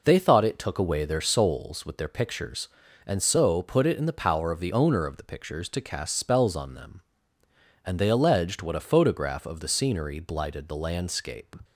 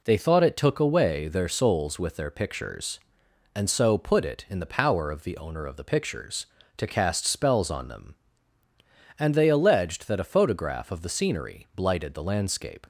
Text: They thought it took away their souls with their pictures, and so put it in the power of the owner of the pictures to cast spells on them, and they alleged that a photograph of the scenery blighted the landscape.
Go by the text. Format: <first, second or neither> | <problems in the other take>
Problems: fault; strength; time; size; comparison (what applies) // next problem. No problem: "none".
second | says "what" for "that"; at 8.6 s